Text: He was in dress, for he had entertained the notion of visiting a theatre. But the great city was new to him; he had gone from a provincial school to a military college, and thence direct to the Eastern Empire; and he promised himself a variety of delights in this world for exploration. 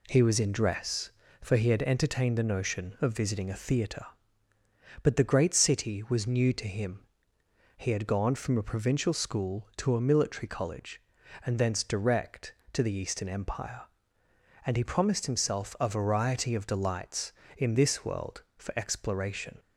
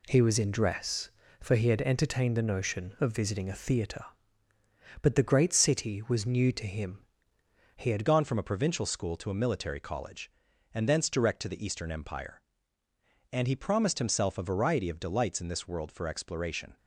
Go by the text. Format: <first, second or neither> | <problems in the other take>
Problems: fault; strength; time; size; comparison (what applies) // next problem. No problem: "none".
first | changes voice at "gone"; from 8.0 s on; 8.7 s long